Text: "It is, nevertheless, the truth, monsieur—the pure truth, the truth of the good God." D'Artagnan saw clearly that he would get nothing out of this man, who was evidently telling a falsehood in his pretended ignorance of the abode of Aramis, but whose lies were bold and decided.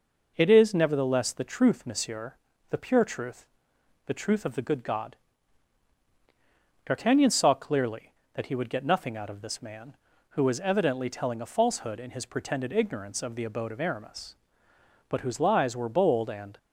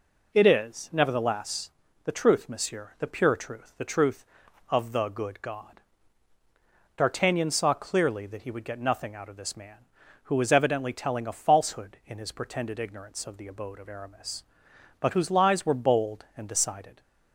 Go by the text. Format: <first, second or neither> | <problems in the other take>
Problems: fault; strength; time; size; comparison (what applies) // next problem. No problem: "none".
second | stops before "decided"; at 16.5 s